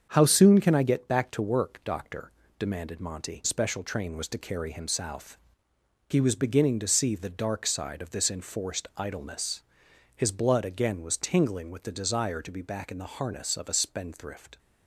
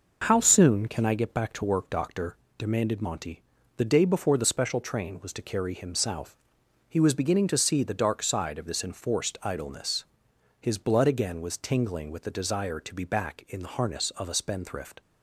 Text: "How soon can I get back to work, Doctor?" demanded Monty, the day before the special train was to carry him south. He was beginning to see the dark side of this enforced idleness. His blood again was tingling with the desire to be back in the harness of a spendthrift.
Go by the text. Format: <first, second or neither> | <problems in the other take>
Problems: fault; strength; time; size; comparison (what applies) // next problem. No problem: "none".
second | starts louder than the rest; until 1.1 s; 7 dB // skips "the day before the"; at 3.4 s